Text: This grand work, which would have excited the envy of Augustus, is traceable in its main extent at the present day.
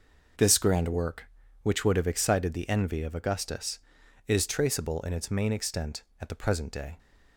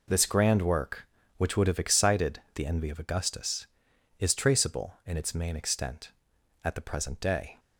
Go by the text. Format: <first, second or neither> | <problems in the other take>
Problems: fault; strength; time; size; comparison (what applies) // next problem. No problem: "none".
neither | none